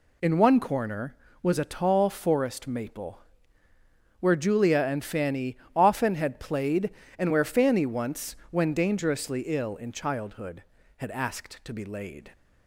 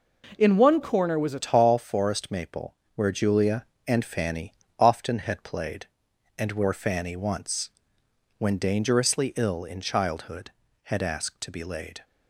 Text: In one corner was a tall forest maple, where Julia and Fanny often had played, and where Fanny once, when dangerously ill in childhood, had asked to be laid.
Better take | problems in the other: first | changes voice at "tall"; from 1.4 s on; 10.6 s long // pauses between "Fanny" and "often"; slight; at 4.5 s; 0.26 s long; slight in the first

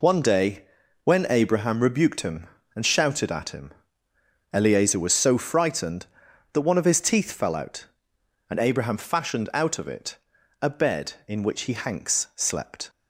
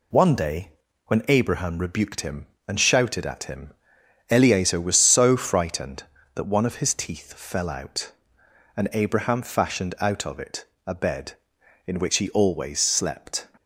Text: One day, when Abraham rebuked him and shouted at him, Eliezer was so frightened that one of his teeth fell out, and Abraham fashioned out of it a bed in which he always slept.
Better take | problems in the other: second | pauses between "it" and "a"; at 10.1 s; 0.42 s long; slight in the second // says "hanks" for "always"; at 11.7 s

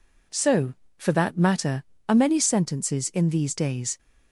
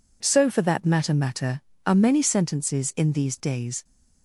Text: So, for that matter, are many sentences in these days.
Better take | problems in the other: first | says "matter" twice; at 1.1 s

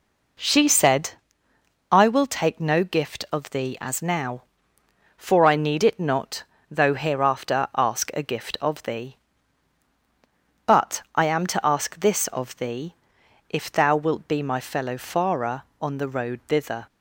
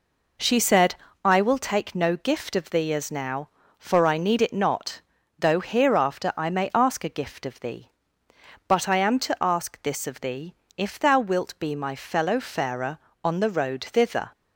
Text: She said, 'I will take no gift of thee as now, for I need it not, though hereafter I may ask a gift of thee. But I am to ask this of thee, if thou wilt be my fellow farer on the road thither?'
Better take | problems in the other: second | skips "I may"; at 7.7 s

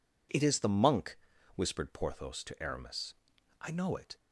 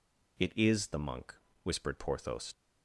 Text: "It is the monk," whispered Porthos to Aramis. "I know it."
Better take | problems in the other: first | stops before "to Aramis I know it"; at 2.5 s

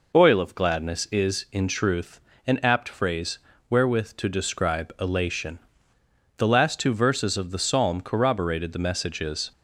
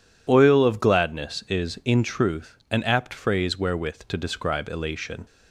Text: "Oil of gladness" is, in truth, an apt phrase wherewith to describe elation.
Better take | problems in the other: second | pauses between "phrase" and "wherewith"; slight; at 3.3 s; 0.32 s long // goes on to say "The last two verses of the psalm corroborated the messages"; strong; from 6.3 s on; 3.1 s long

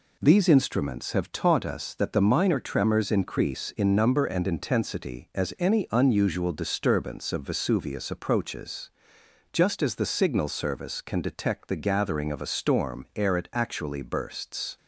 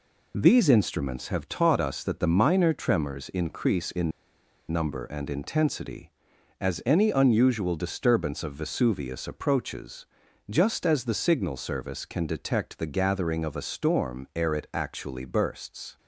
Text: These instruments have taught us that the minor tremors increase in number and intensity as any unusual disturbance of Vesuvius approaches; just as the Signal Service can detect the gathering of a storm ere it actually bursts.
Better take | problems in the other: first | pauses between "in" and "number"; noticeable; at 4.1 s; 0.60 s long

